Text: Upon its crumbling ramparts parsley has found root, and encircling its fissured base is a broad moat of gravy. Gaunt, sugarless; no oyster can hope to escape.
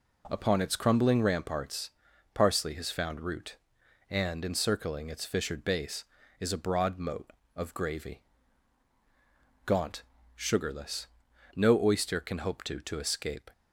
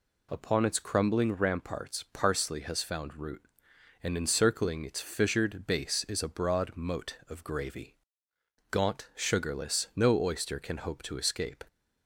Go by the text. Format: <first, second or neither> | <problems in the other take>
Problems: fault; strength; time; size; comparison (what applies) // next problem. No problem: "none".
second | pauses between "ramparts" and "parsley"; at 1.8 s; 0.44 s long // says "to" twice; at 12.7 s